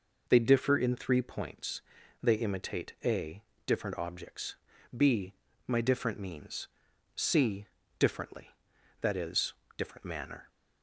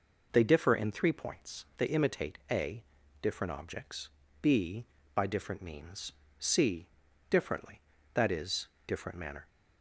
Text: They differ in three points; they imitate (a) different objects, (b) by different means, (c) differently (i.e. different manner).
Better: second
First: says "my" for "by"; at 5.6 s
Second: none

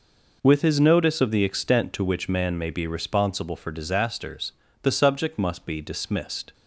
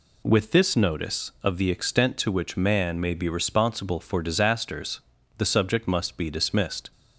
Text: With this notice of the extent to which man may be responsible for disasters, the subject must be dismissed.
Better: second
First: says "his" for "this"; at 0.6 s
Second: none

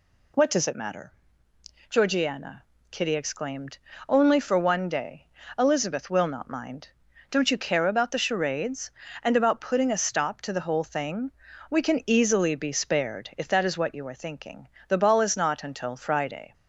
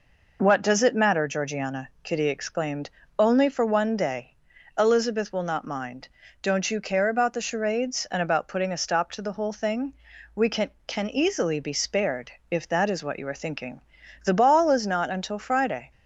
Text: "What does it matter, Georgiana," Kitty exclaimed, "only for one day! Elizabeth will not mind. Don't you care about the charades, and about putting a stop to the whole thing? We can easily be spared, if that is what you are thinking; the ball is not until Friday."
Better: first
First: none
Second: says "can" twice; at 10.8 s

